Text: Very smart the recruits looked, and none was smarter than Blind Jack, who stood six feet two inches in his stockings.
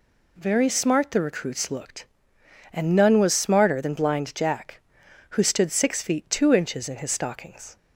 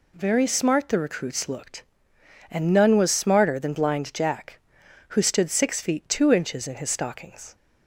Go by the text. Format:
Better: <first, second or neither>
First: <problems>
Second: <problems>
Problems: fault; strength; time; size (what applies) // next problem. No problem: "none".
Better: neither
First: none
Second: none